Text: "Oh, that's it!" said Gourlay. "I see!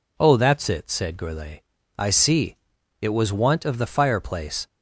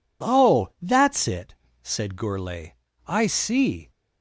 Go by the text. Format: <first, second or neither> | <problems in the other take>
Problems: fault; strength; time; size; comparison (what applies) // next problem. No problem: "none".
second | goes on to say "It was want of the fireplace"; from 3.0 s on; 1.6 s long